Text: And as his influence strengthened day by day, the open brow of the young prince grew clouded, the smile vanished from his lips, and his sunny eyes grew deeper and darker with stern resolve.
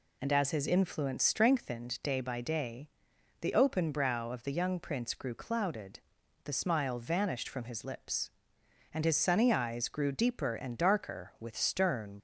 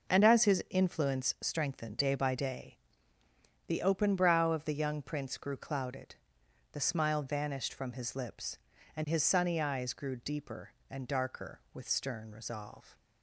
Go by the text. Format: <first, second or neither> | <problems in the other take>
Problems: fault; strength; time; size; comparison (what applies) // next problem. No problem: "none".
second | stops before "resolve"; at 12.1 s